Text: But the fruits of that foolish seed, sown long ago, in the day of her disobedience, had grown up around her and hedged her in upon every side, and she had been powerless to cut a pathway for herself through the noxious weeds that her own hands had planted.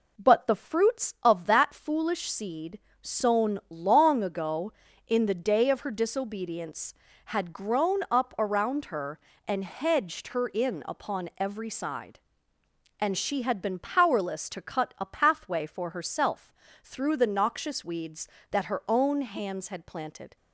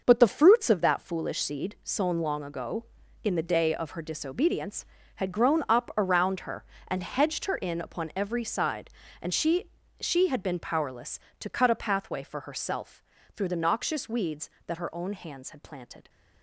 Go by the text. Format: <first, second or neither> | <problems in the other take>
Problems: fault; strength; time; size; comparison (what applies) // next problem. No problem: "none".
first | says "she" twice; at 10.0 s // pauses between "herself" and "through"; slight; at 13.0 s; 0.32 s long; slight in the first